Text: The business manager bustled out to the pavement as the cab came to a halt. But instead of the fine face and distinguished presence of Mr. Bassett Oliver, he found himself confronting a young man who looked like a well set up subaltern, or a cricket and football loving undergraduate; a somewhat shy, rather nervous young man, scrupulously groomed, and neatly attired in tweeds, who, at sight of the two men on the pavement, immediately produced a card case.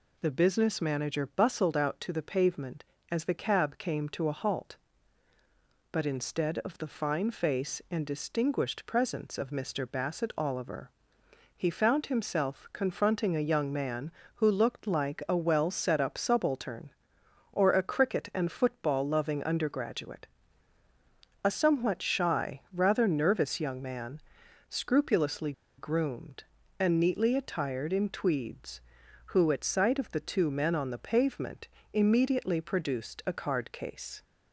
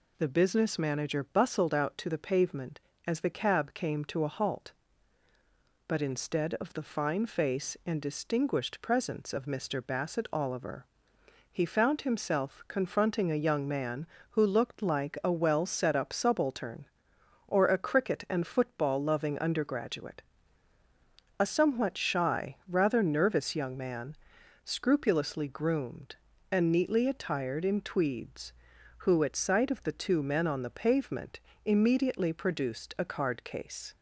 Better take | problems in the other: second | pauses between "scrupulously" and "groomed"; slight; at 25.5 s; 0.26 s long

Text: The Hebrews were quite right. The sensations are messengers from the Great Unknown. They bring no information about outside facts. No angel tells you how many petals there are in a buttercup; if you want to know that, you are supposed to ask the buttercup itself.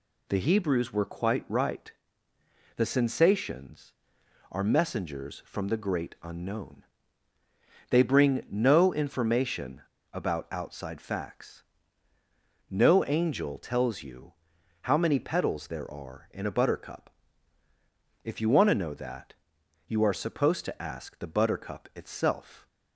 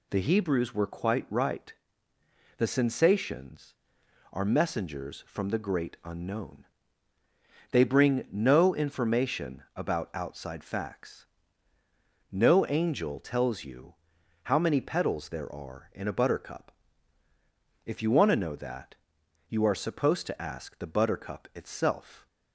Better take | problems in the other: second | pauses between "information" and "about"; slight; at 9.8 s; 0.30 s long // pauses between "you" and "how"; noticeable; at 14.3 s; 0.48 s long; noticeable in the second

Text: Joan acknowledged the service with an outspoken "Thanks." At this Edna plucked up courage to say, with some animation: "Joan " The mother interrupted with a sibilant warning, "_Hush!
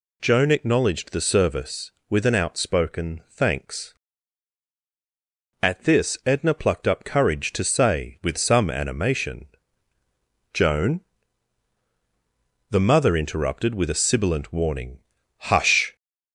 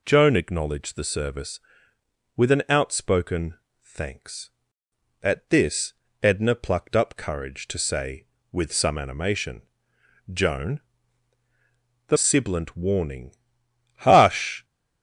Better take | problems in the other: first | pauses between "outspoken" and "Thanks"; slight; at 3.5 s; 0.30 s long // pauses between "this" and "Edna"; slight; at 5.9 s; 0.30 s long // skips "mother interrupted with a"; at 12.1 s

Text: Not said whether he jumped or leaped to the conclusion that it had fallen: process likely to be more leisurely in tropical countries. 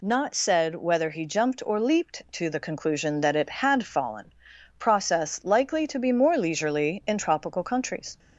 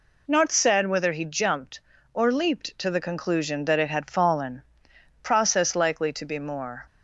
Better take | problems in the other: first | stops before "leisurely in tropical countries"; at 6.8 s

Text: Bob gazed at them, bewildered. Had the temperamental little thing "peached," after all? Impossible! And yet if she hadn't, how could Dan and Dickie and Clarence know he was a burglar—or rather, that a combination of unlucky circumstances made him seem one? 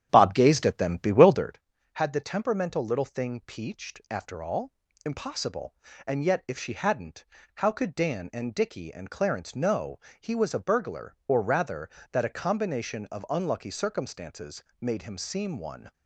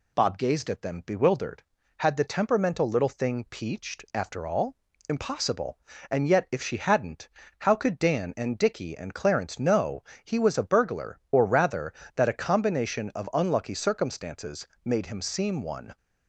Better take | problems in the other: second | starts louder than the rest; strong; until 1.6 s; 9.5 dB // pauses between "know" and "he"; slight; at 10.0 s; 0.18 s long; slight in the second // pauses between "circumstances" and "made"; slight; at 14.6 s; 0.16 s long; slight in the second

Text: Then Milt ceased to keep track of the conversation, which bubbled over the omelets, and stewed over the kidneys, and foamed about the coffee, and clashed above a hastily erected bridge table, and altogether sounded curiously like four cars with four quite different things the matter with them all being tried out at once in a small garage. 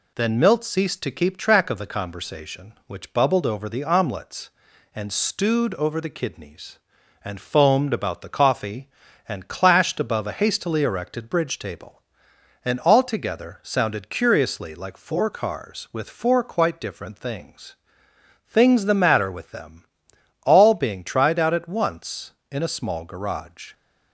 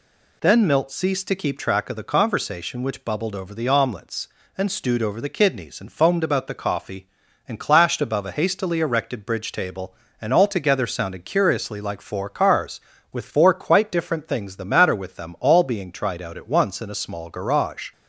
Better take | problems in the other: second | says "things" twice; at 18.4 s // pauses between "them" and "all"; noticeable; at 19.8 s; 0.58 s long

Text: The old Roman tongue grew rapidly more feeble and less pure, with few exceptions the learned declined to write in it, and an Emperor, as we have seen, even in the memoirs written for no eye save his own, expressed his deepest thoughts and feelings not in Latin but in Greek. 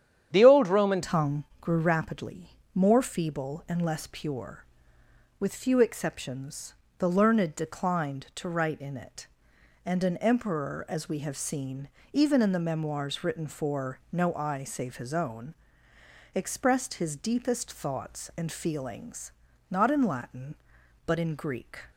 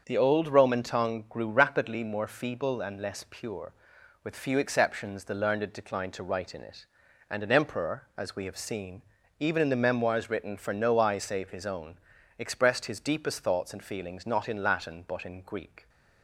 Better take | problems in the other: second | starts louder than the rest; strong; until 1.3 s; 9.5 dB; also in the second // changes voice at "tongue"; from 1.0 s on; 20.7 s long // pauses between "tongue" and "grew"; slight; at 1.4 s; 0.16 s long // pauses between "rapidly" and "more"; slight; at 2.4 s; 0.26 s long // pauses between "exceptions" and "the"; slight; at 6.7 s; 0.24 s long // pauses between "feelings" and "not"; at 19.3 s; 0.40 s long

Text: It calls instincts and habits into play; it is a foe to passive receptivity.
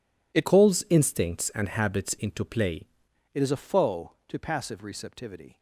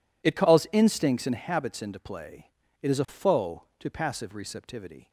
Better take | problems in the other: second | changes voice from "calls" to "play"; from 0.4 to 2.8 s; 2.4 s long

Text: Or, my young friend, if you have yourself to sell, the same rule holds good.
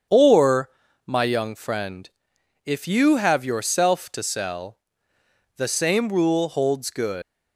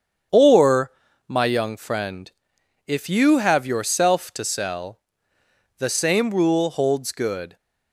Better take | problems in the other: second | starts louder than the rest; strong; until 1.4 s; 7.5 dB; strong in the second // leaves "good" unfinished; at 7.2 s; 120 ms

